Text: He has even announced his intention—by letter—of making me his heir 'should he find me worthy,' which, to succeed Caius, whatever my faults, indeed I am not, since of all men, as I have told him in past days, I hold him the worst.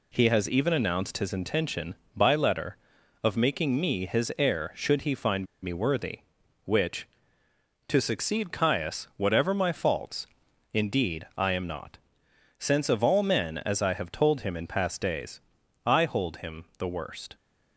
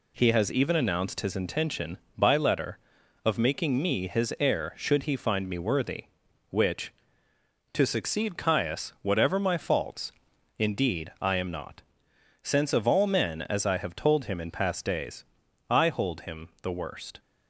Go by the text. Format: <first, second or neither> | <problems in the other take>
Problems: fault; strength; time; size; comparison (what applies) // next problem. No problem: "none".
second | pauses between "find" and "me"; slight; at 5.4 s; 0.16 s long